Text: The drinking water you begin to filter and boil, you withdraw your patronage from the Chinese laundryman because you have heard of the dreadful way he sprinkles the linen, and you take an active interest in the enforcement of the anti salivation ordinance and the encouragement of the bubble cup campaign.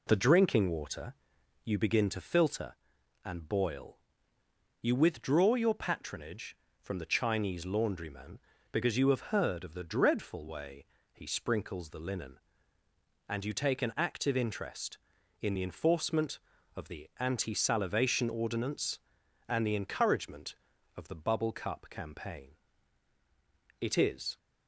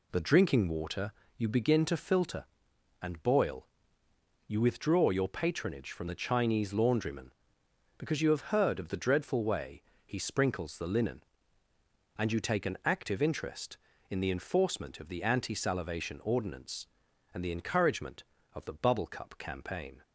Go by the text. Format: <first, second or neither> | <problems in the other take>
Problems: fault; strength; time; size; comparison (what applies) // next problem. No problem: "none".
second | pauses between "water" and "you"; noticeable; at 1.1 s; 0.50 s long; slight in the second // pauses between "way" and "he"; slight; at 10.8 s; 0.26 s long; slight in the second // goes on to say "It is"; from 23.8 s on; 0.56 s long